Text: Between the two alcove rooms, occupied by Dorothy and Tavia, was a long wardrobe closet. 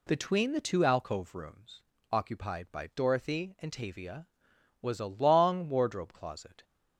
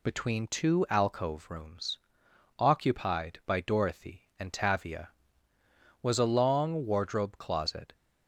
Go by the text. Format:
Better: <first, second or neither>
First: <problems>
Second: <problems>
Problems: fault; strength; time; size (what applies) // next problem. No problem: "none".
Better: first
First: none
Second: skips "the"; at 0.4 s